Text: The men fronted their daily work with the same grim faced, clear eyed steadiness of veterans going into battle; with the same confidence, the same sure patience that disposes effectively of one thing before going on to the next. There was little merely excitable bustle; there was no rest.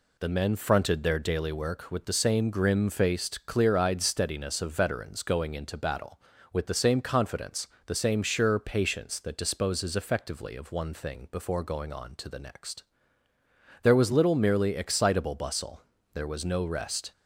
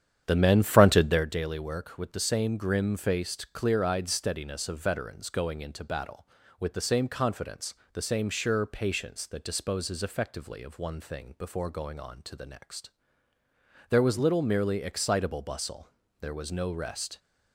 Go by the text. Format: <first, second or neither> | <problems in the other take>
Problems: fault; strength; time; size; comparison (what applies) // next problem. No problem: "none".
first | starts louder than the rest; strong; until 1.3 s; 9.5 dB